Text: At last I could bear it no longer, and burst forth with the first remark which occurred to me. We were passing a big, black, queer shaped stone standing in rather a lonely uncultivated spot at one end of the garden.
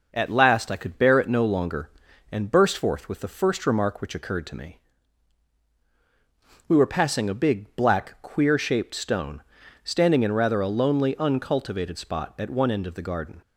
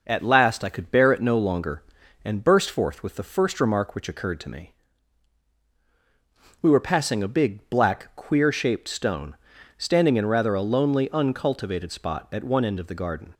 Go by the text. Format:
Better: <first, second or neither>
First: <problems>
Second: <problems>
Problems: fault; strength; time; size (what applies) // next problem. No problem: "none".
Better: neither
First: pauses between "stone" and "standing"; noticeable; at 9.4 s; 0.46 s long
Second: pauses between "stone" and "standing"; noticeable; at 9.3 s; 0.46 s long